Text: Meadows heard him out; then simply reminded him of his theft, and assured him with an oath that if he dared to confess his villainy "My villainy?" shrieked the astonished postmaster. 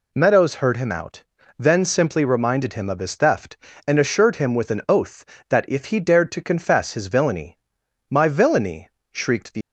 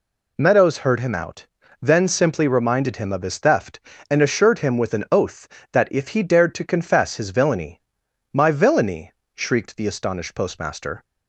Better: second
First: pauses between "villainy" and "My"; noticeable; at 7.5 s; 0.52 s long // stops before "astonished postmaster"; at 9.6 s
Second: pauses between "villainy" and "My"; noticeable; at 7.8 s; 0.52 s long

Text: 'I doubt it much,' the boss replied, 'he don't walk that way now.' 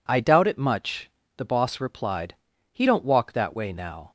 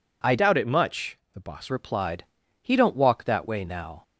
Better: first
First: none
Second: changes voice from "doubt" to "boss"; from 0.3 to 1.7 s; 1.4 s long

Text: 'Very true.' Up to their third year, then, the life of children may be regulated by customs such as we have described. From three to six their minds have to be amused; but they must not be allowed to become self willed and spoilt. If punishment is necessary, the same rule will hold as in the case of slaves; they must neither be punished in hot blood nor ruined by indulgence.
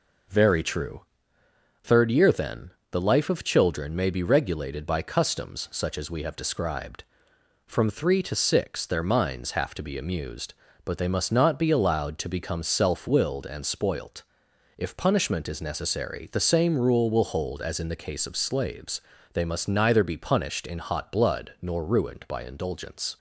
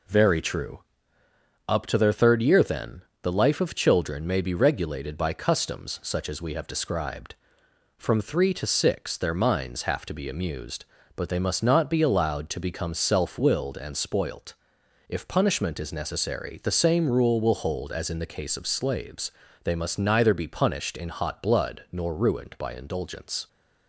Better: second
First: skips "Up to their"; at 1.4 s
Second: none

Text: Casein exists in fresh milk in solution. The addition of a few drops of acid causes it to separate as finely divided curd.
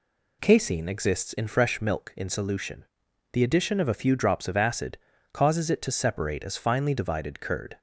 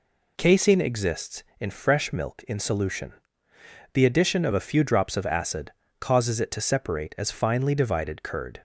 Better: neither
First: pauses between "acid" and "causes"; slight; at 4.9 s; 0.36 s long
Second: pauses between "acid" and "causes"; slight; at 5.7 s; 0.28 s long

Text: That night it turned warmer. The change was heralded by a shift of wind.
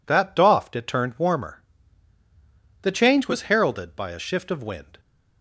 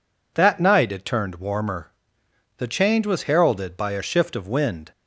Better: second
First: says "doffed" for "night"; at 0.3 s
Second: none

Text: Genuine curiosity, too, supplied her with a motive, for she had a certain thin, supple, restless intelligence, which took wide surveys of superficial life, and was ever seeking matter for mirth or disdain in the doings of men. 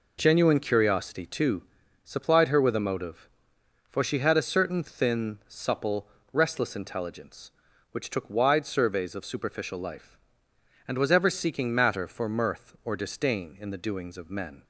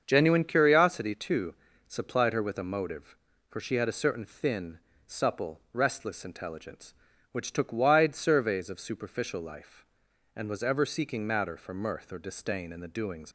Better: first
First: none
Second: starts louder than the rest; until 1.0 s; 7 dB // stops before "of men"; at 13.2 s

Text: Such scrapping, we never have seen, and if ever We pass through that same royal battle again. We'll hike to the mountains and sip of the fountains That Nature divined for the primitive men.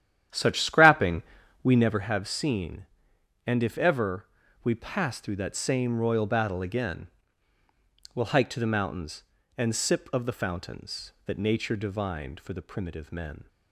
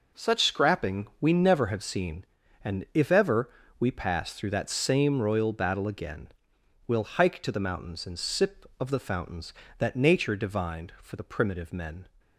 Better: second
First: starts louder than the rest; strong; until 2.1 s; 10.5 dB // pauses between "ever" and "We"; slight; at 4.2 s; 0.36 s long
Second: pauses between "ever" and "We"; slight; at 3.4 s; 0.30 s long

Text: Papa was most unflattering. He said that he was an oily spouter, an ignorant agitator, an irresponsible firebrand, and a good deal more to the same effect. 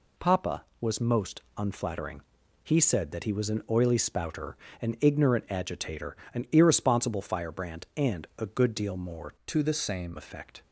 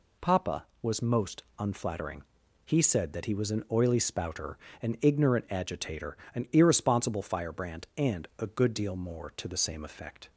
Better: second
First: pauses between "most" and "unflattering"; slight; at 1.4 s; 0.16 s long // changes voice from "to" to "same"; from 9.4 to 10.1 s; 0.7 s long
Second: pauses between "most" and "unflattering"; slight; at 1.4 s; 0.16 s long

